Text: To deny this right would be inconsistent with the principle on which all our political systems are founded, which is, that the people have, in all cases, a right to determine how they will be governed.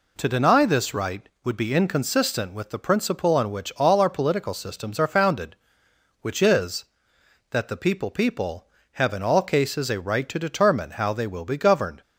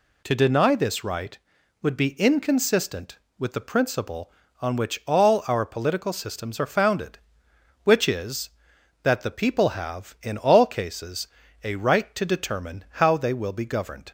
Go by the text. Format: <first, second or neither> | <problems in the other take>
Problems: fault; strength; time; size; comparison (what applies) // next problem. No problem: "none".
second | says "people" twice; at 8.1 s